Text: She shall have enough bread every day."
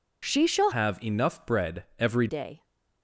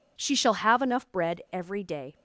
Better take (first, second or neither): second